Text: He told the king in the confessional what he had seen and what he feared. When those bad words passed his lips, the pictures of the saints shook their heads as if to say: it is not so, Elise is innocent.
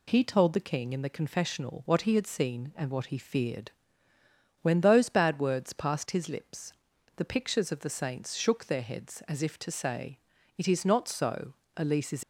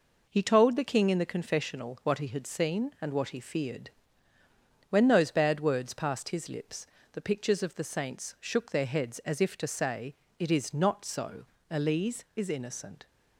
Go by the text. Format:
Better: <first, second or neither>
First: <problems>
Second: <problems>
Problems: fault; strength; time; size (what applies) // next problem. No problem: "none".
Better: second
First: stops before "innocent"; at 12.2 s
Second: none